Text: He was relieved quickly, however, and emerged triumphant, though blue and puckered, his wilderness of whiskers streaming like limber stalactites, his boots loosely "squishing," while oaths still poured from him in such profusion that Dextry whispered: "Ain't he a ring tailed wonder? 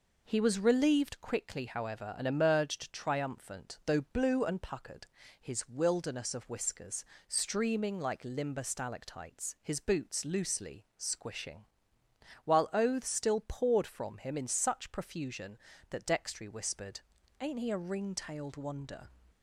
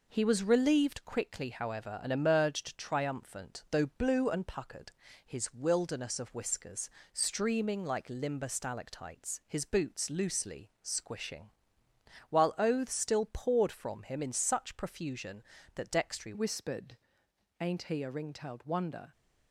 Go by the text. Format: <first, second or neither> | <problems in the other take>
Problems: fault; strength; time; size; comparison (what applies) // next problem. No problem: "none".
first | pauses between "whiskers" and "streaming"; slight; at 6.8 s; 0.24 s long; slight in the first // changes voice at "whispered"; from 16.3 s on; 2.8 s long